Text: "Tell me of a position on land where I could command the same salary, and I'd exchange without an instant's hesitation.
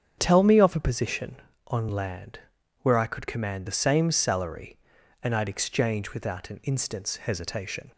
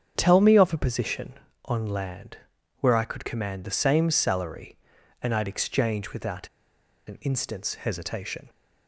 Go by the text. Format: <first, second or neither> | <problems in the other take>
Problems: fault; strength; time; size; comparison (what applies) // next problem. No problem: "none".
first | starts louder than the rest; strong; until 1.1 s; 8 dB; strong in the first // pauses between "land" and "where"; at 2.3 s; 0.40 s long; also in the first // pauses between "without" and "an"; noticeable; at 6.4 s; 0.59 s long